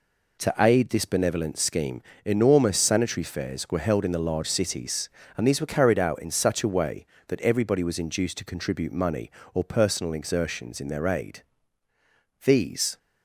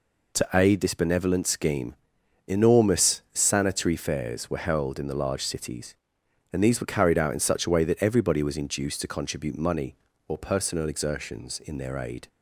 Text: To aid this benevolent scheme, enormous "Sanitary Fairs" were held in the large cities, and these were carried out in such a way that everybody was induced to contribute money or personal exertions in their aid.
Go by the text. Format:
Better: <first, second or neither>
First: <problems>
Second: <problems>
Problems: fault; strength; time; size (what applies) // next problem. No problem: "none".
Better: second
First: goes on to say "These"; from 12.4 s on; 0.54 s long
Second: none